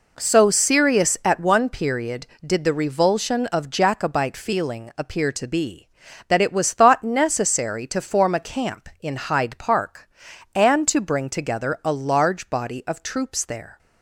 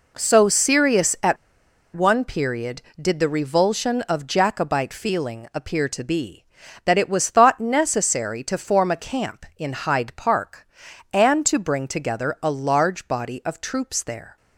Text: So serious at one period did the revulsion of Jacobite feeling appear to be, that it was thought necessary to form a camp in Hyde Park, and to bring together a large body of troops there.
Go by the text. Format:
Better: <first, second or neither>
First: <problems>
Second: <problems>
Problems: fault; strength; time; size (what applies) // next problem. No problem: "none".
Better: first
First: none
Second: pauses between "at" and "one"; noticeable; at 1.3 s; 0.59 s long